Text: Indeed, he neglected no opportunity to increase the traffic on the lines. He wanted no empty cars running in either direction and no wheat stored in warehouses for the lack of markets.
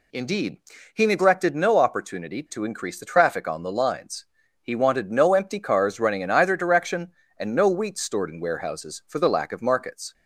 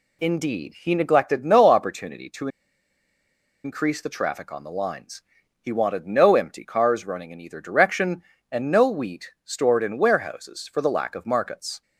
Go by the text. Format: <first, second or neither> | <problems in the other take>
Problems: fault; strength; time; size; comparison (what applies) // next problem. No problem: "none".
first | pauses between "to" and "increase"; at 2.4 s; 1.1 s long